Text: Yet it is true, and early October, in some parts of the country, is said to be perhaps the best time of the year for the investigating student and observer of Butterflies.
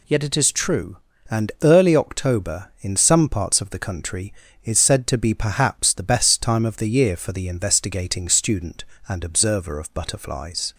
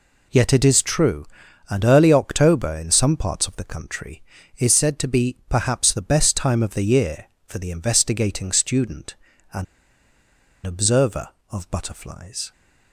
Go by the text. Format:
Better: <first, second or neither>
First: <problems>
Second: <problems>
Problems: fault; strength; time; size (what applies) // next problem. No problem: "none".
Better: first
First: none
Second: pauses between "and" and "observer"; at 9.6 s; 1.0 s long